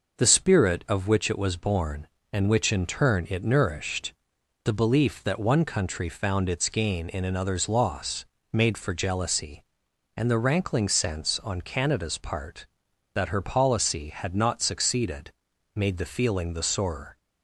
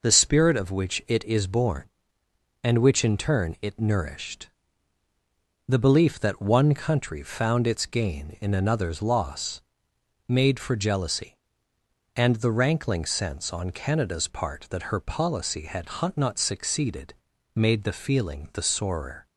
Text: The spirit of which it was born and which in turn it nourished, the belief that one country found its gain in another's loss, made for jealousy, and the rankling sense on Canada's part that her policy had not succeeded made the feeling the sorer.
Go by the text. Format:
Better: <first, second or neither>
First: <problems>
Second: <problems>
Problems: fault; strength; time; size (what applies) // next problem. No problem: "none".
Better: first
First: pauses between "succeeded" and "made"; at 15.3 s; 0.42 s long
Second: says "is" for "was"; at 1.2 s // pauses between "had" and "not"; slight; at 15.8 s; 0.30 s long // pauses between "succeeded" and "made"; at 17.1 s; 0.42 s long